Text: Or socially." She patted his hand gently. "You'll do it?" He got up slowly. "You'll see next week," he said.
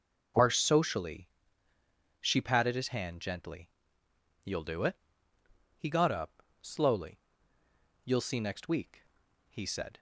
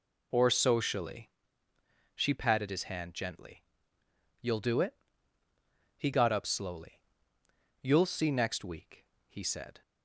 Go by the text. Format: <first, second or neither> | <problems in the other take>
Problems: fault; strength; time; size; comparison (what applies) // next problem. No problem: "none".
second | says "Are" for "Or"; at 0.3 s // pauses between "up" and "slowly"; slight; at 6.4 s; 0.18 s long